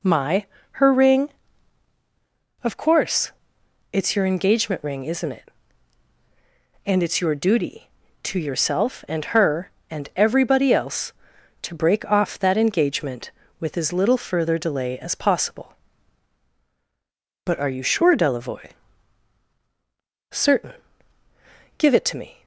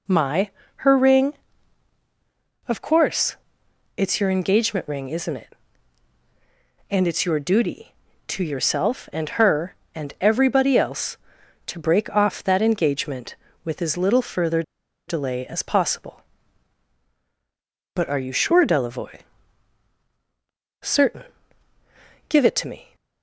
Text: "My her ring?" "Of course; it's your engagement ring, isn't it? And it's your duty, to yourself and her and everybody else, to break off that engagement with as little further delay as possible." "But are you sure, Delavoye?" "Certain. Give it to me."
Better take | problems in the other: first | pauses between "My" and "her"; slight; at 0.5 s; 0.26 s long; slight in the first // pauses between "further" and "delay"; noticeable; at 14.6 s; 0.46 s long

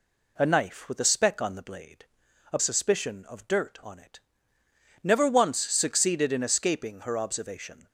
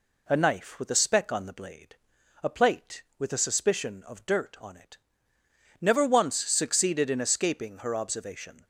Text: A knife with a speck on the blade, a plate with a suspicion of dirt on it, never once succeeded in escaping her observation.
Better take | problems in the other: second | skips "plate with a"; at 2.5 s

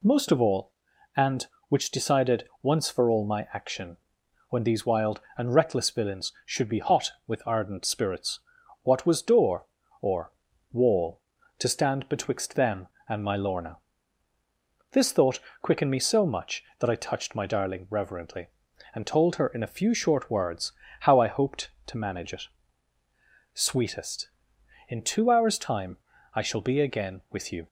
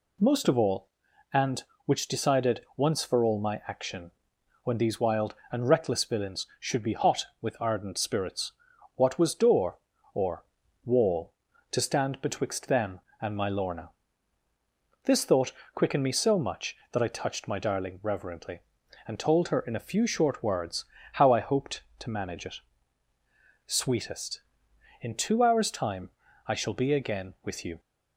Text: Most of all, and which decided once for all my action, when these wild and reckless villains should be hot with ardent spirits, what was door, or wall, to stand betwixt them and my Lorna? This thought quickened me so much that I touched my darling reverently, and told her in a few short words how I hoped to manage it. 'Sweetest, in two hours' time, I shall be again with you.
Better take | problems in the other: neither | pauses between "or" and "wall"; the same in both // pauses between "thought" and "quickened"; slight; the same in both // pauses between "words" and "how"; slight; the same in both

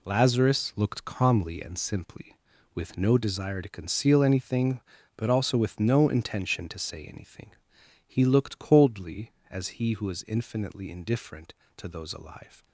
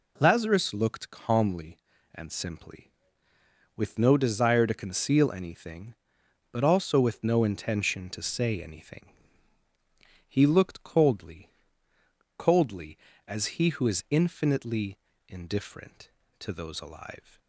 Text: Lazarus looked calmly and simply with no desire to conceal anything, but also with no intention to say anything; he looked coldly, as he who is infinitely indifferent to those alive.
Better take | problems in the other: first | says "coldly" twice; at 12.3 s // pauses between "infinitely" and "indifferent"; slight; at 14.9 s; 0.30 s long

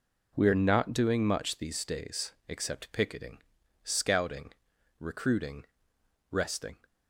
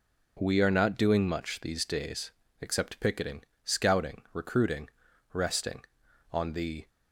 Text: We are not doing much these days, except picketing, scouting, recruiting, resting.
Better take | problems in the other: first | goes on to say "On the"; from 6.3 s on; 0.56 s long

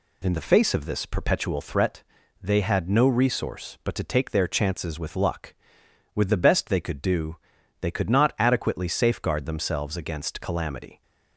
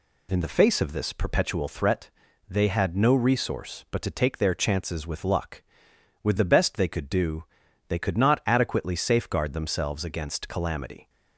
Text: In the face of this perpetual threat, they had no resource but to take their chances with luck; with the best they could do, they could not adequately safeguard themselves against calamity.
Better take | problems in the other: neither | none

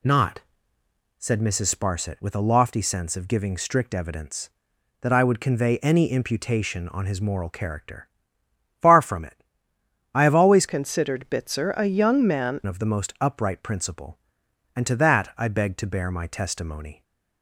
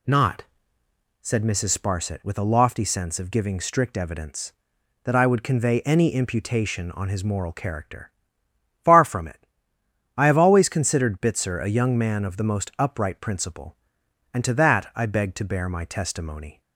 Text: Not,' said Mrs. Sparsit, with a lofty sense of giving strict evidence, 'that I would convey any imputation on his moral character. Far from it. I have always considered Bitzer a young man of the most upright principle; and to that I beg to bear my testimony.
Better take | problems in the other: second | changes voice from "considered" to "man"; from 10.6 to 12.5 s; 1.9 s long

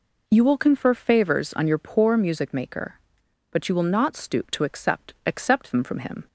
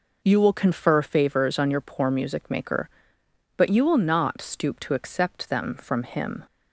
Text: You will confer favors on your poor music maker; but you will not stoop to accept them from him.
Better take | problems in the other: second | says "accept" twice; at 5.2 s

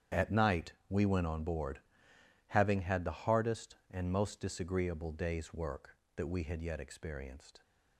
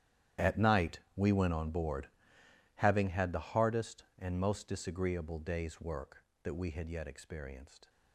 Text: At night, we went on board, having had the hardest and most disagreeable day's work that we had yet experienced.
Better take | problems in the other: first | gets quieter; strong; throughout; 17.5 dB // starts louder than the rest; strong; until 1.5 s; 10.5 dB; strong in the first

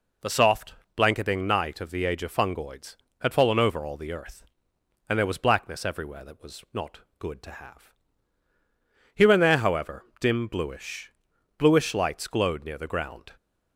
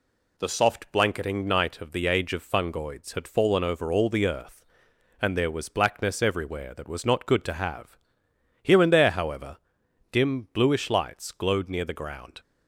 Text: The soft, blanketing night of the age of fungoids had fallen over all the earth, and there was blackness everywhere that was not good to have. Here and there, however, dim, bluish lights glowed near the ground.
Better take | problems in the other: second | pauses between "not" and "good"; slight; at 7.0 s; 0.18 s long // says "bluish" twice; at 11.5 s

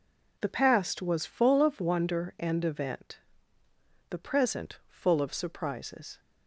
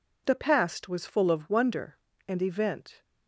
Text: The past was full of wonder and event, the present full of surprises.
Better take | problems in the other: first | stops before "the present full of surprises"; at 3.0 s

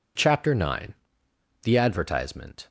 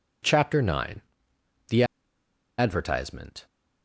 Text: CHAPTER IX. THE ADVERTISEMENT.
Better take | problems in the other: first | pauses between "THE" and "ADVERTISEMENT"; noticeable; at 1.8 s; 0.74 s long

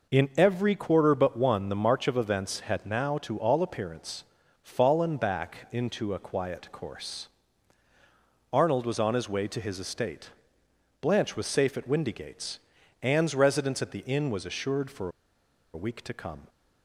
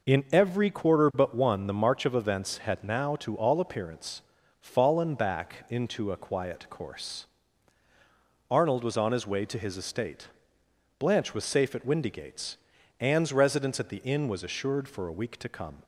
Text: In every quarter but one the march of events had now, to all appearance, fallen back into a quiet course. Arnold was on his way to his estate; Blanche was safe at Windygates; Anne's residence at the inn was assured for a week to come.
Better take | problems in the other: second | pauses between "for" and "a"; noticeable; at 15.0 s; 0.63 s long

